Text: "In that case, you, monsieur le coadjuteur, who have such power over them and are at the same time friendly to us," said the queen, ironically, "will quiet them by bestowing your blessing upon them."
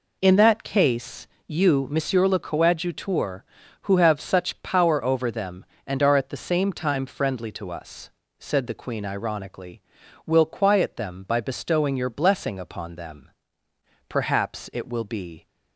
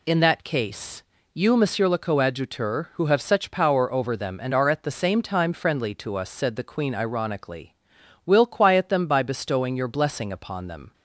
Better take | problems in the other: second | goes on to say "Perhaps it will be"; from 14.0 s on; 1.3 s long

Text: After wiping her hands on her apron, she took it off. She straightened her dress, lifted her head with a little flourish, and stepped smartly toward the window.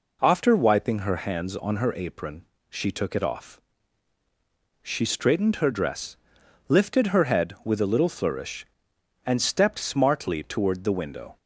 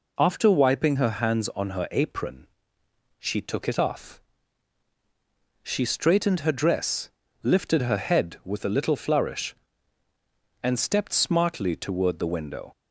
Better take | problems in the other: neither | none

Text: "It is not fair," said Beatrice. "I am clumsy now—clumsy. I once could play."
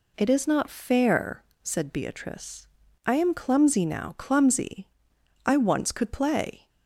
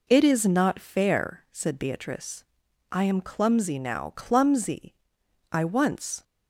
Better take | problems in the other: first | stops before "could play"; at 6.2 s

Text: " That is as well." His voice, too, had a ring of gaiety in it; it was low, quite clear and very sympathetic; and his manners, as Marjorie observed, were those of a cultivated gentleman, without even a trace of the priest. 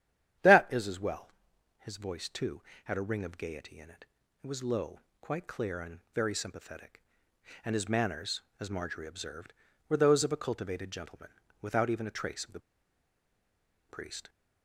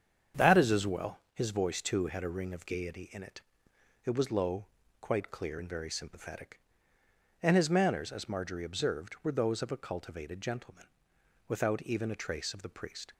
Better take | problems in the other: second | starts louder than the rest; strong; until 1.9 s; 10 dB; strong in the second // pauses between "and" and "very"; slight; at 5.9 s; 0.16 s long // pauses between "the" and "priest"; strong; at 12.6 s; 1.2 s long

